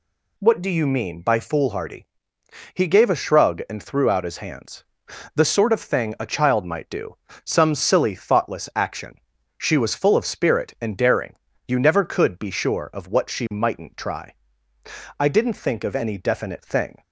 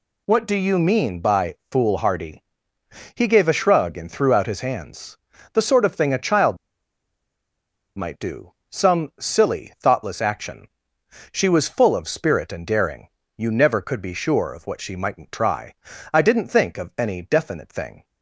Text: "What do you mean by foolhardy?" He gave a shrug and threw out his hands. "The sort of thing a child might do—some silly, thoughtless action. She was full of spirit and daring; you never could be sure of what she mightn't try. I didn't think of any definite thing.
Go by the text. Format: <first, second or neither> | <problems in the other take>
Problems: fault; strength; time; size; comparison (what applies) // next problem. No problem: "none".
first | pauses between "child" and "might"; strong; at 6.5 s; 1.3 s long